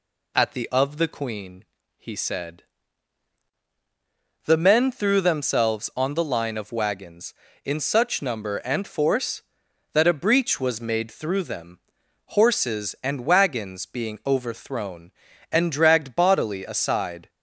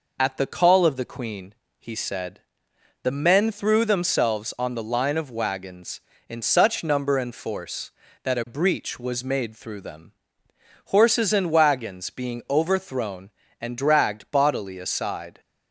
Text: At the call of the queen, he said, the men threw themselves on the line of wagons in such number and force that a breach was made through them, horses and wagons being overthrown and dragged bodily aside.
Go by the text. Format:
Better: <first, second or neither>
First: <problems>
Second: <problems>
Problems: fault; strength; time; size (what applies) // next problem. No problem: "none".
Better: second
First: skips "call"; at 0.6 s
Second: none